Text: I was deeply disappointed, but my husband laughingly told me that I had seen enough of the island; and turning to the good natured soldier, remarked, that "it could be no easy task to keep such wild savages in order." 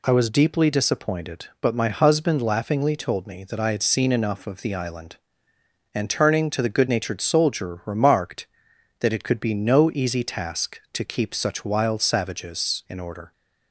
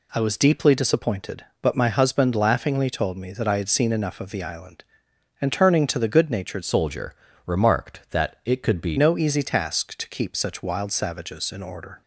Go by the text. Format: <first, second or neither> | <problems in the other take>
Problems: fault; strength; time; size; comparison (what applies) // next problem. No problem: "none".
first | changes voice from "soldier" to "be"; from 6.6 to 8.9 s; 2.3 s long